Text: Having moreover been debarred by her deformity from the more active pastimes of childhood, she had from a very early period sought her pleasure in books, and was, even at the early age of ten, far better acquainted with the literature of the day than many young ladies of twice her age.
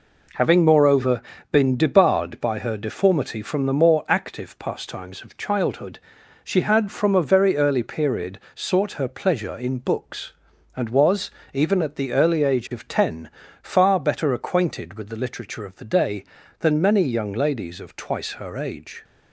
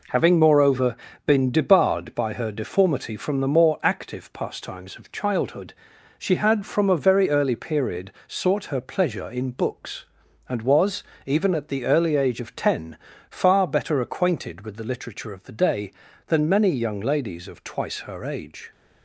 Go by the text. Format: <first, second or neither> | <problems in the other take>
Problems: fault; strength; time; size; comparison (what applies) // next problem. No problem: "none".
neither | pauses between "moreover" and "been"; slight; the same in both // pauses between "period" and "sought"; slight; the same in both